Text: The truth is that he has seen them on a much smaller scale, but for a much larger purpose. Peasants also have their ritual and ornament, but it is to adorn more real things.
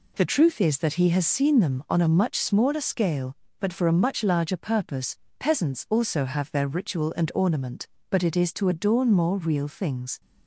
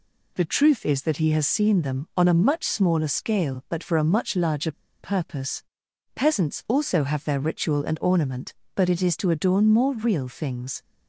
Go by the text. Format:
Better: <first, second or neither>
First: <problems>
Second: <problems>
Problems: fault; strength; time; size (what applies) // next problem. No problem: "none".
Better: first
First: none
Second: pauses between "larger" and "purpose"; slight; at 4.7 s; 0.29 s long